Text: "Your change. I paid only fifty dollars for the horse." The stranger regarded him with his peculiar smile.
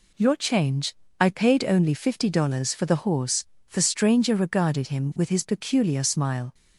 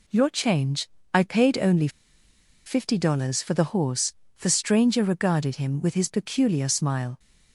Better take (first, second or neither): first